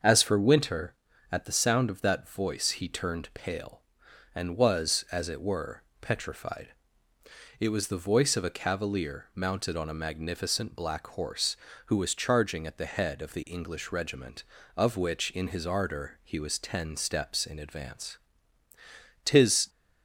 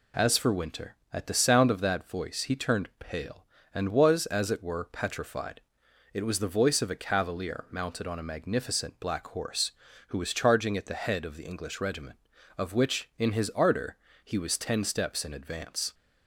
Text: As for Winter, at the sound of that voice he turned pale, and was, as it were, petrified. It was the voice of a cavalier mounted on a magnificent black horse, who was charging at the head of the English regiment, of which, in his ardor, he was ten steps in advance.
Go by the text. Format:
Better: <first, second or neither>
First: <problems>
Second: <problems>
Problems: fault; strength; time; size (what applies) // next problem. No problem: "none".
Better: second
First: starts louder than the rest; until 1.3 s; 6.5 dB // goes on to say "Tis"; slight; from 19.2 s on; 0.46 s long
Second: none